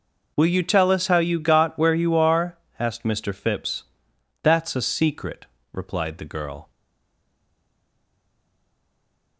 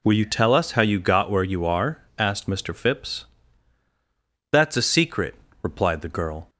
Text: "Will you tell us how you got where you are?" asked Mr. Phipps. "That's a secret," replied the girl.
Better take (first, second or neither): second